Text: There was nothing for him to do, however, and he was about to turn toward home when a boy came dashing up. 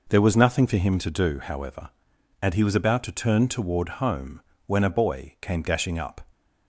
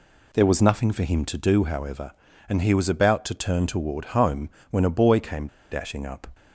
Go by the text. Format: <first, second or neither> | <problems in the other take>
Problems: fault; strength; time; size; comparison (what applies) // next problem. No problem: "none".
first | pauses between "home" and "when"; slight; at 4.4 s; 0.20 s long; slight in the first // pauses between "came" and "dashing"; slight; at 5.4 s; 0.23 s long